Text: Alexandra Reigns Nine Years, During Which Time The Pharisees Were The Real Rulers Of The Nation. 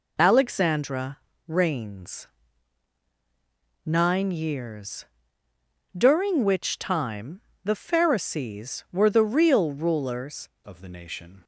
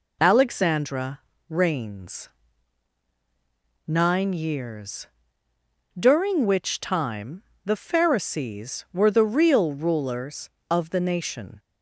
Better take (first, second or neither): second